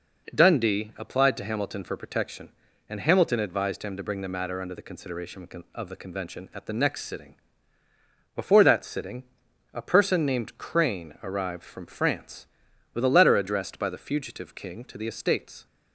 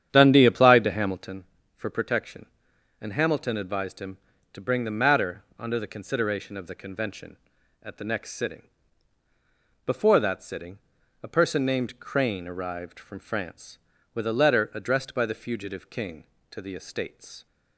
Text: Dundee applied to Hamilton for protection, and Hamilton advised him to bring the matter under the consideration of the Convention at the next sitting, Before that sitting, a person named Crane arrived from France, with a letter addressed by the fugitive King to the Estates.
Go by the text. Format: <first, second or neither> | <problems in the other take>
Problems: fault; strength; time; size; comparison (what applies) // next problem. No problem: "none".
first | starts louder than the rest; strong; until 1.4 s; 9 dB